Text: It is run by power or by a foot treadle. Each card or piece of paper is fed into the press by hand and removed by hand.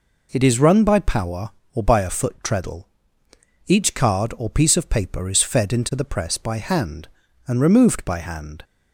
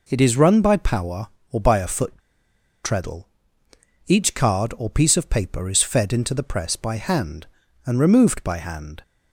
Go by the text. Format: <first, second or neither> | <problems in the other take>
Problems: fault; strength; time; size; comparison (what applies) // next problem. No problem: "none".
first | pauses between "foot" and "treadle"; noticeable; at 2.1 s; 0.70 s long